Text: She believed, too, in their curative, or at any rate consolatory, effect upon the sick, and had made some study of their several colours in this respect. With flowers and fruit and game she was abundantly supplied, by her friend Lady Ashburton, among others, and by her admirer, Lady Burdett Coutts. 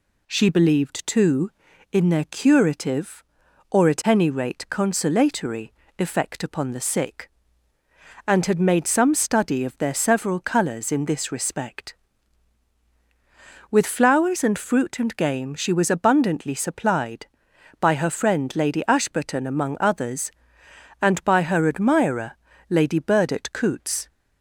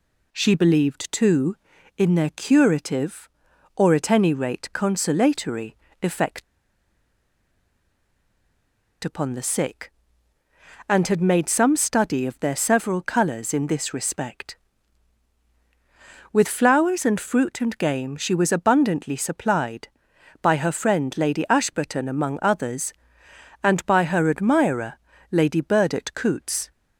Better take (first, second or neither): first